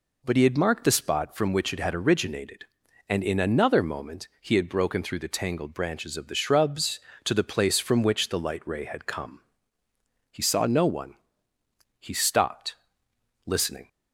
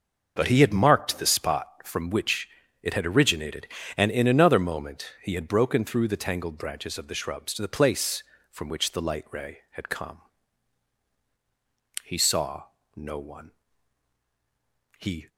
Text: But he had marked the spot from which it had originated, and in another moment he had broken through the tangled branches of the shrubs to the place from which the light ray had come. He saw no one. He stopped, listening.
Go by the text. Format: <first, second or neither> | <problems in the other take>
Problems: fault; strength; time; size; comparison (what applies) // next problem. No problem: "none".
first | starts louder than the rest; noticeable; until 1.3 s; 6 dB // pauses between "which" and "it"; slight; at 2.4 s; 0.36 s long // pauses between "saw" and "no"; slight; at 12.6 s; 0.30 s long // stops before "stopped listening"; at 15.2 s